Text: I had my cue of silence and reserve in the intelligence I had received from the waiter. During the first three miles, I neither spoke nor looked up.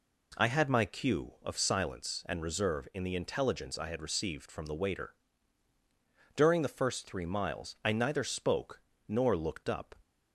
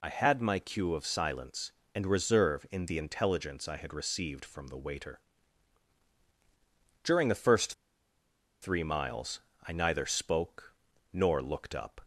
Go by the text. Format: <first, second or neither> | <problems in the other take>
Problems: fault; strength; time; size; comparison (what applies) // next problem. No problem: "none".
first | pauses between "first" and "three"; noticeable; at 7.7 s; 0.89 s long // pauses between "spoke" and "nor"; at 10.7 s; 0.38 s long; slight in the first